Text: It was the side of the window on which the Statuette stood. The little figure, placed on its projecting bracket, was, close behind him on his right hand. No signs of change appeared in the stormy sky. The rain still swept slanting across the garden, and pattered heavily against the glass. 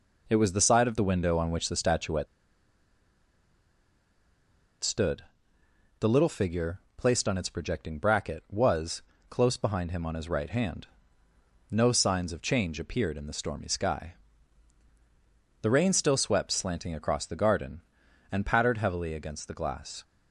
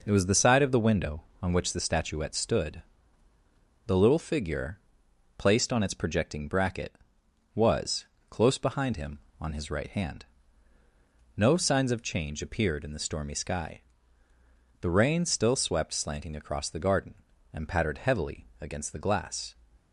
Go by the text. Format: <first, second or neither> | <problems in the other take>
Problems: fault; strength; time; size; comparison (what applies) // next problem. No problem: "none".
second | pauses between "Statuette" and "stood"; strong; at 2.2 s; 2.5 s long